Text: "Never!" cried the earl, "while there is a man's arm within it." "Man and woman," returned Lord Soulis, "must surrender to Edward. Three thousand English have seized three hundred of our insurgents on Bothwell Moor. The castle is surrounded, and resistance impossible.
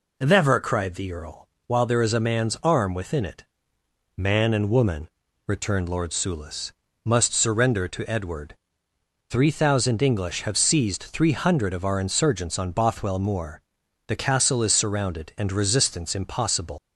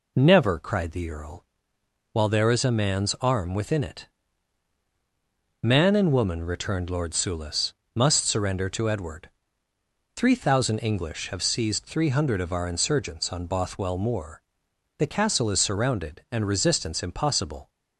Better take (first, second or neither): second